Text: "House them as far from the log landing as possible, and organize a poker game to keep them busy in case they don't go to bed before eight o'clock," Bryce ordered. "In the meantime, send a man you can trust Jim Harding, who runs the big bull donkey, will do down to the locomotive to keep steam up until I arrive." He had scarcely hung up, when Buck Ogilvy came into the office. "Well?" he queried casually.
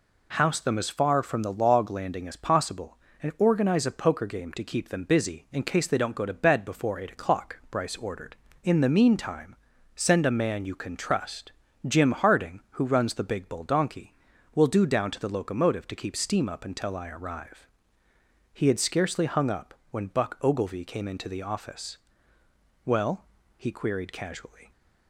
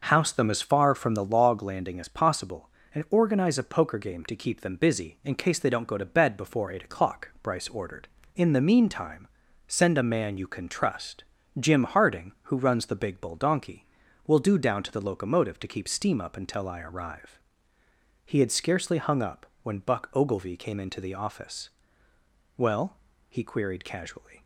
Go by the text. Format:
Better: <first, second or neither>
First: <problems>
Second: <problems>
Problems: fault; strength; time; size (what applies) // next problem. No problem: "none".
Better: first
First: pauses between "trust" and "Jim"; slight; at 11.5 s; 0.34 s long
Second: starts louder than the rest; noticeable; until 1.4 s; 6 dB // pauses between "trust" and "Jim"; slight; at 11.2 s; 0.34 s long